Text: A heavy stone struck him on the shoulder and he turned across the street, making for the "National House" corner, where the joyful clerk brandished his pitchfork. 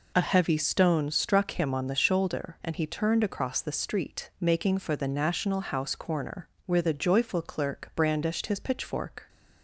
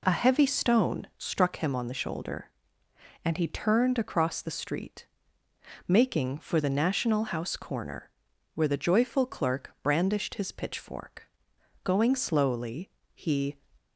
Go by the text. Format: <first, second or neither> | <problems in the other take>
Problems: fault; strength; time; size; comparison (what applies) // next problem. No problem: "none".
first | goes on to say "Going slowly he"; strong; from 11.8 s on; 1.7 s long